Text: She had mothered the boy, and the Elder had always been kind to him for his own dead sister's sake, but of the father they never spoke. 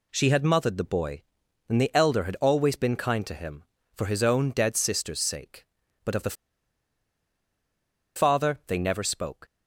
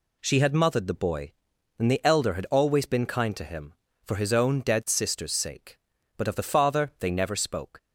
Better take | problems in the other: second | pauses between "the" and "father"; strong; at 6.3 s; 1.8 s long

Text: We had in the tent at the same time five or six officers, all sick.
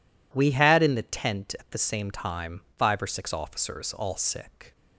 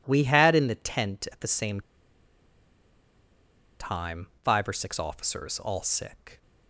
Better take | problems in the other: first | pauses between "same" and "time"; strong; at 1.8 s; 1.9 s long // pauses between "time" and "five"; slight; at 4.2 s; 0.16 s long; slight in the first

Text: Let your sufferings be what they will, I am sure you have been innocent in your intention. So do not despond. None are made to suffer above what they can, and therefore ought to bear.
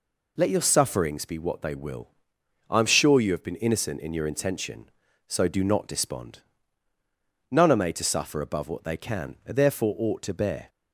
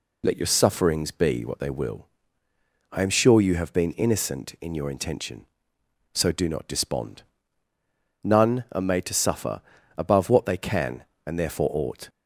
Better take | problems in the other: first | pauses between "suffer" and "above"; at 9.6 s; 0.38 s long // stops before "to bear"; at 12.0 s

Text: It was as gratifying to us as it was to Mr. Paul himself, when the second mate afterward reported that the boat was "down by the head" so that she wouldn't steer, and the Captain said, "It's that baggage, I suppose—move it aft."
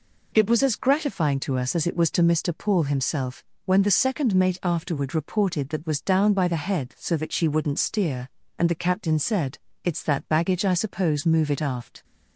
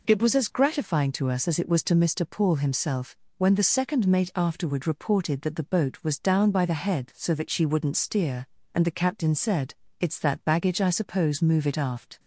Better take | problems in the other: second | skips "the boat"; at 5.8 s

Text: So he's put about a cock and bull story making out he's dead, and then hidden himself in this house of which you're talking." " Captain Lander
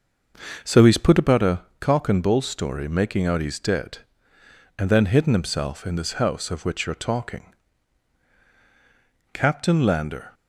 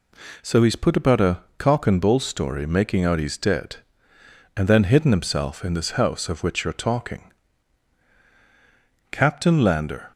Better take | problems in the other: second | starts louder than the rest; until 1.4 s; 6.5 dB // pauses between "a" and "cock"; slight; at 1.6 s; 0.18 s long; slight in the second

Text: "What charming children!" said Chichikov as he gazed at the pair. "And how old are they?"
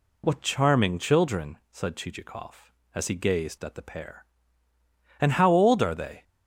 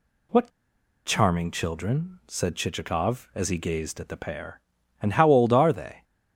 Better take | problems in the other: first | pauses between "What" and "charming"; noticeable; at 0.4 s; 0.57 s long

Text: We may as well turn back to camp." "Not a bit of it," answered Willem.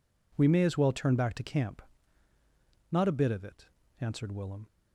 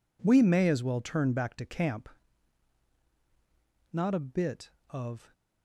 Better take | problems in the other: first | stops before "it answered Willem"; at 5.3 s

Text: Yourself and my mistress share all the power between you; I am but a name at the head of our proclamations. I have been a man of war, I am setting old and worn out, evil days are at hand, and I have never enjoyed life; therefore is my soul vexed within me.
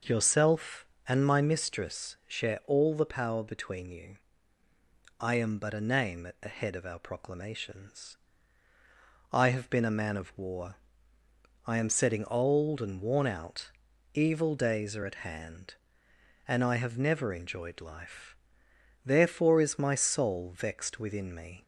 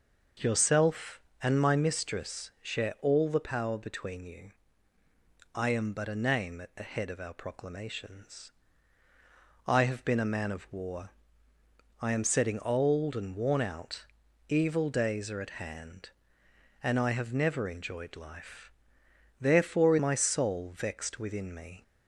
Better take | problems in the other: first | skips "is"; at 19.9 s

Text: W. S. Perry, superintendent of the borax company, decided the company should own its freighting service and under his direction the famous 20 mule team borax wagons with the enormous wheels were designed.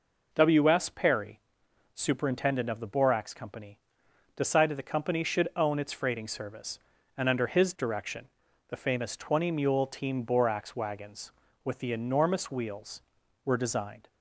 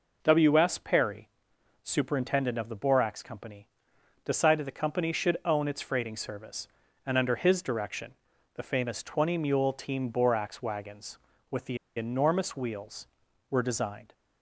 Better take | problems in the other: first | pauses between "direction" and "the"; at 8.1 s; 0.42 s long; also in the first // pauses between "the" and "enormous"; slight; at 11.7 s; 0.19 s long

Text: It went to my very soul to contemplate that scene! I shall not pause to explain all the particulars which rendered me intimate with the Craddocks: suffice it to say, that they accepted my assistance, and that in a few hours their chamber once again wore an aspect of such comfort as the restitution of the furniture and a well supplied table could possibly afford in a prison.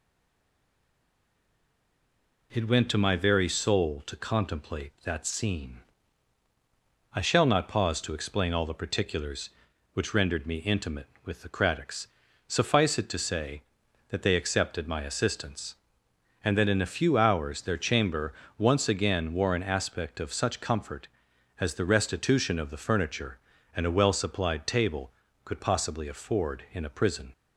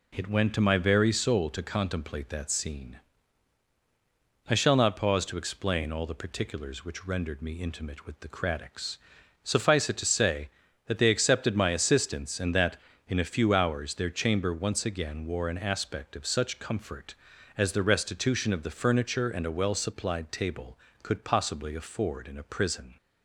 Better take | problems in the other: second | stays silent before the first word; until 2.5 s; 2.5 s long // pauses between "chamber" and "once"; slight; at 18.3 s; 0.24 s long

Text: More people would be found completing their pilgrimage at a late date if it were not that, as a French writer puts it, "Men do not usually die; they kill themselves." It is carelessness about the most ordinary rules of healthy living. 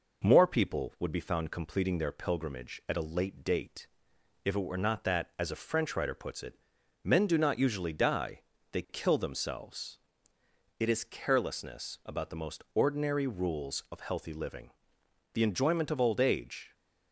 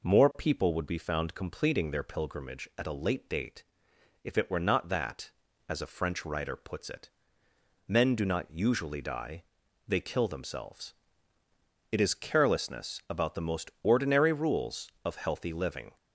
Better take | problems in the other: second | pauses between "date" and "if"; noticeable; at 3.8 s; 0.56 s long; noticeable in the second // goes on to say "The enjoyment of old age"; from 15.3 s on; 1.4 s long

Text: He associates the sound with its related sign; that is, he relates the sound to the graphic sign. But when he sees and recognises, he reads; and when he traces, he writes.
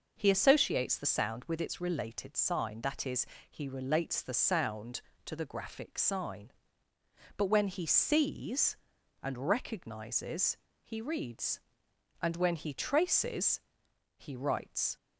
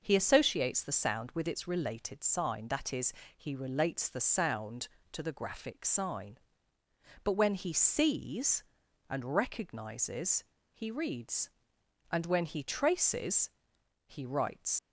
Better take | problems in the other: first | leaves "writes" unfinished; at 14.7 s; 65 ms

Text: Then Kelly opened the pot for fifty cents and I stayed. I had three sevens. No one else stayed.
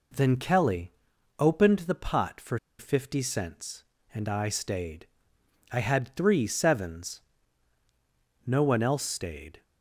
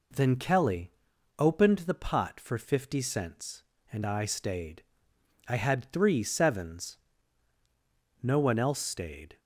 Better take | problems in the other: second | pauses between "Kelly" and "opened"; noticeable; at 0.9 s; 0.46 s long; noticeable in the second // pauses between "for" and "fifty"; slight; at 2.5 s; 0.20 s long

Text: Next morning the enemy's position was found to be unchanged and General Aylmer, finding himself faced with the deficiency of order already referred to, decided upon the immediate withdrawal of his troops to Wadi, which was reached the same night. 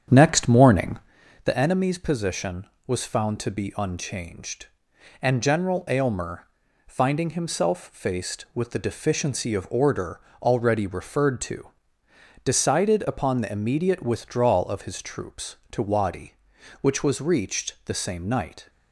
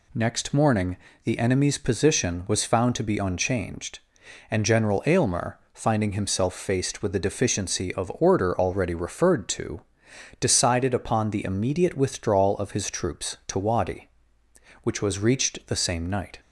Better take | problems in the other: second | starts louder than the rest; strong; until 1.2 s; 8 dB // pauses between "morning" and "the"; noticeable; at 0.9 s; 0.46 s long; slight in the second // pauses between "order" and "already"; slight; at 10.1 s; 0.22 s long

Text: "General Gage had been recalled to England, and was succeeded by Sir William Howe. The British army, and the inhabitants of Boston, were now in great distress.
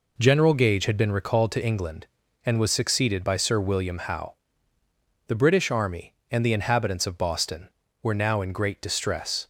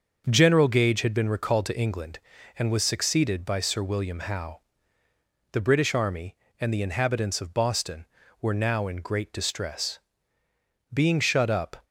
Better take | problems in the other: first | starts louder than the rest; until 1.2 s; 6 dB // goes on to say "Being shut up"; noticeable; from 10.9 s on; 0.92 s long

